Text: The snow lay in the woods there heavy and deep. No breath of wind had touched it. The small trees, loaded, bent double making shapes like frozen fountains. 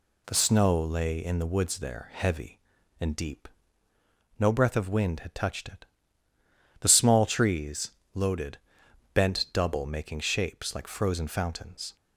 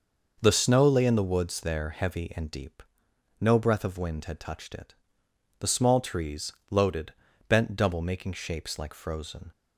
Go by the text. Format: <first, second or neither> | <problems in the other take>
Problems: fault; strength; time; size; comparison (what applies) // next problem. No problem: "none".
first | stops before "fountains"; at 9.5 s